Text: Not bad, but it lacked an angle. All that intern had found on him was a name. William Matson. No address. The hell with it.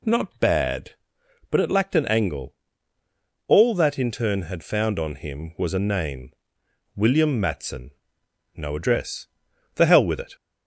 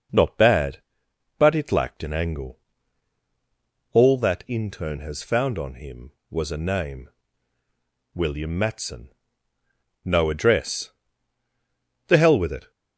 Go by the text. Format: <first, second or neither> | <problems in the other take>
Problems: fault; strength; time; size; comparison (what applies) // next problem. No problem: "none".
first | says "has" for "had"; at 5.0 s